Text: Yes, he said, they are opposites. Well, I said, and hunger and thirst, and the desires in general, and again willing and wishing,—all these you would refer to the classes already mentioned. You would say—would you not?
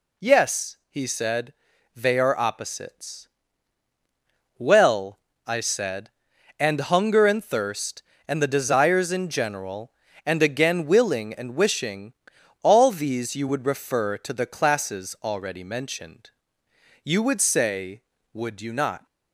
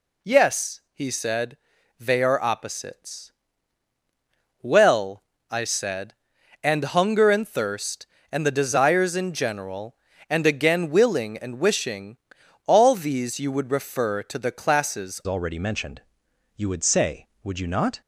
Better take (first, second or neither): first